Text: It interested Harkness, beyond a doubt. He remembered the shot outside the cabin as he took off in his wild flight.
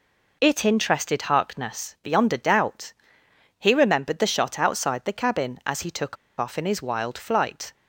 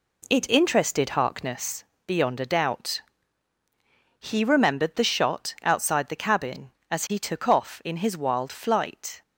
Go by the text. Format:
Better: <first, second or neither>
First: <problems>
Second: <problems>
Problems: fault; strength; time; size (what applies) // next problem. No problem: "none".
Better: second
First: pauses between "took" and "off"; slight; at 6.1 s; 0.23 s long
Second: none